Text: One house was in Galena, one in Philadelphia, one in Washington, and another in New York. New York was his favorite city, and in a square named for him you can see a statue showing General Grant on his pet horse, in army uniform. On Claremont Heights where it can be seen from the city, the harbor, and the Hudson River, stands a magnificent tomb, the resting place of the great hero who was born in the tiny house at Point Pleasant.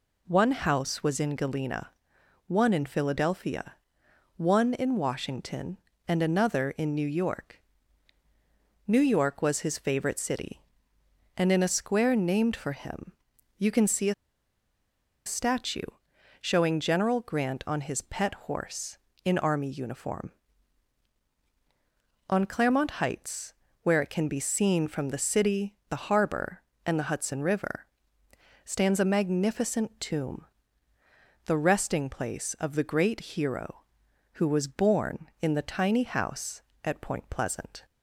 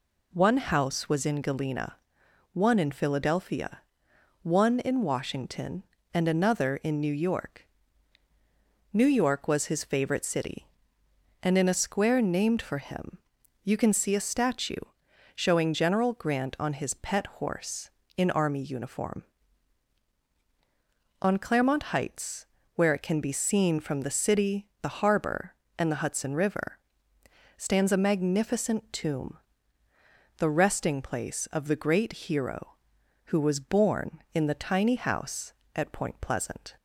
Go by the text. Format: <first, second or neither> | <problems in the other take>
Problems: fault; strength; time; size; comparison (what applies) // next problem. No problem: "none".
second | pauses between "him" and "you"; noticeable; at 13.1 s; 0.48 s long; noticeable in the second // pauses between "a" and "statue"; at 14.1 s; 1.1 s long // pauses between "statue" and "showing"; noticeable; at 15.8 s; 0.56 s long; noticeable in the second // pauses between "Heights" and "where"; slight; at 23.5 s; 0.30 s long; slight in the second